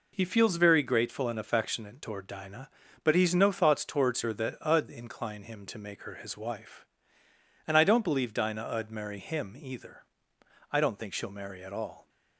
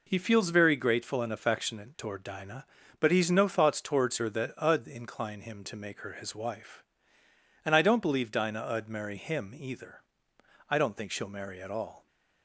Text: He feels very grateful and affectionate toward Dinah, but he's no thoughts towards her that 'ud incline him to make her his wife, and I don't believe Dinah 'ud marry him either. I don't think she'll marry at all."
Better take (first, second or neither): neither